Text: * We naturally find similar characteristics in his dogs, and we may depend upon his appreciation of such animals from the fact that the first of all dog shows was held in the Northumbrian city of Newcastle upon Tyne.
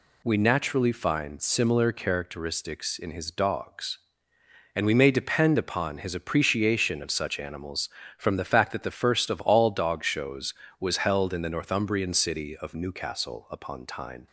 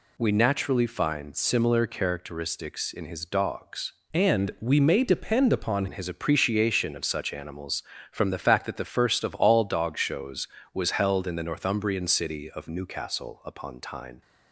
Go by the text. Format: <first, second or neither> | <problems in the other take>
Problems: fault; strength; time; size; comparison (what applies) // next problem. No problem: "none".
first | changes voice from "and" to "upon"; from 4.1 to 5.8 s; 1.7 s long